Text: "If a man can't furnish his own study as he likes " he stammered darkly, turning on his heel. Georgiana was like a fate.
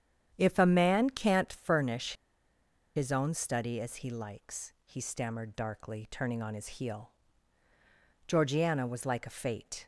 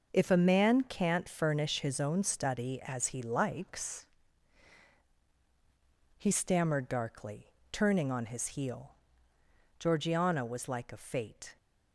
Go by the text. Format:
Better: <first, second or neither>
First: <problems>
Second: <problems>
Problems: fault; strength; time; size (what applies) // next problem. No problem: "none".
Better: second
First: starts louder than the rest; strong; until 1.3 s; 9 dB // pauses between "furnish" and "his"; noticeable; at 2.1 s; 0.82 s long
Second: starts louder than the rest; until 1.1 s; 6.5 dB